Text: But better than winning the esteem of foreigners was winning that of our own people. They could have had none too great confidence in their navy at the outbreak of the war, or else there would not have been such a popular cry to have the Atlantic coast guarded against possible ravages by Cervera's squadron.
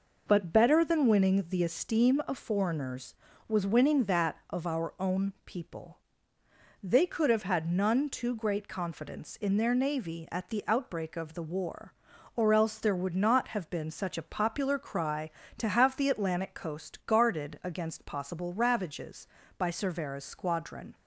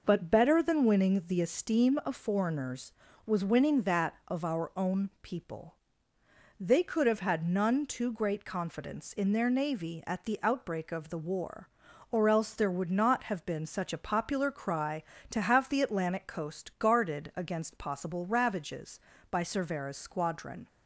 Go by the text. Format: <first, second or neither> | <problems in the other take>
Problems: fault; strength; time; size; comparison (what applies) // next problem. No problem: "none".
neither | none